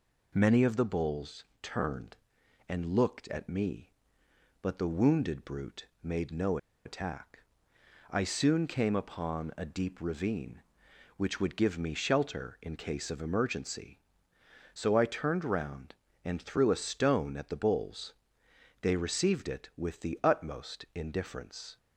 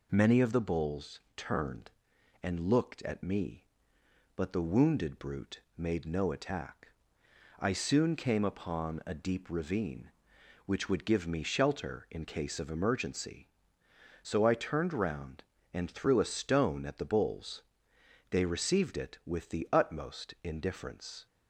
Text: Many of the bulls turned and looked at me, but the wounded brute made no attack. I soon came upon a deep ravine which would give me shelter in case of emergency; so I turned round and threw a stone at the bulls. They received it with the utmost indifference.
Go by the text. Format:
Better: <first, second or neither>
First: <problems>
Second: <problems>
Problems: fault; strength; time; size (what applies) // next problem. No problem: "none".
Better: second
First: pauses between "bulls" and "turned"; slight; at 1.4 s; 0.18 s long // pauses between "brute" and "made"; slight; at 5.8 s; 0.16 s long // pauses between "no" and "attack"; slight; at 6.5 s; 0.27 s long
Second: pauses between "bulls" and "turned"; slight; at 1.1 s; 0.16 s long // pauses between "brute" and "made"; slight; at 5.5 s; 0.16 s long